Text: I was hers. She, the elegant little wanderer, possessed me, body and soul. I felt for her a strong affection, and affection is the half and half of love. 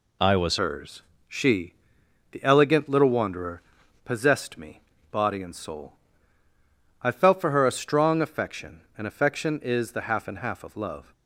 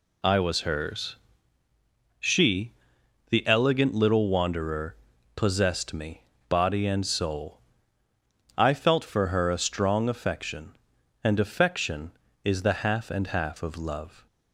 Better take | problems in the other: second | changes voice at "hers"; from 0.5 s on; 10.6 s long

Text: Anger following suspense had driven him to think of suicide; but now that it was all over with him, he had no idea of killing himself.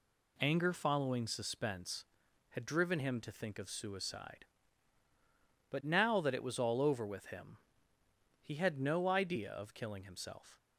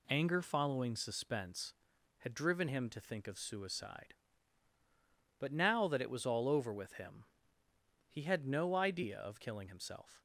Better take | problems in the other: neither | none

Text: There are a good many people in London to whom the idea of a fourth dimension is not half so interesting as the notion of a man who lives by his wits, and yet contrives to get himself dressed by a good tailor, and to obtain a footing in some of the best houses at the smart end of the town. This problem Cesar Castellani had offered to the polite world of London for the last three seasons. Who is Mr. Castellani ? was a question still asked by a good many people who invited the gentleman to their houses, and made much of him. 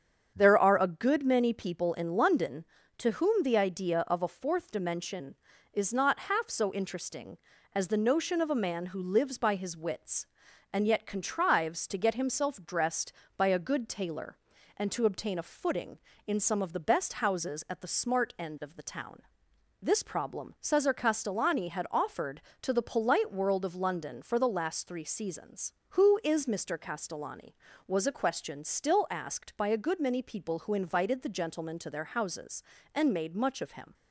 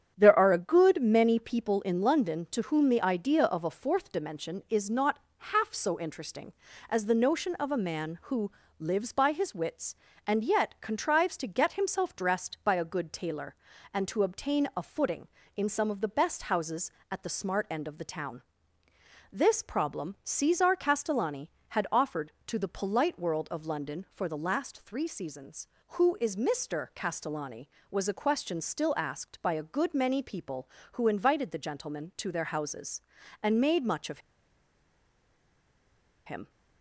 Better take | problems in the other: first | starts louder than the rest; strong; until 1.1 s; 9 dB; strong in the first // pauses between "not" and "half"; slight; at 5.1 s; 0.20 s long // pauses between "who" and "lives"; slight; at 8.5 s; 0.26 s long // pauses between "of" and "him"; strong; at 34.1 s; 2.0 s long

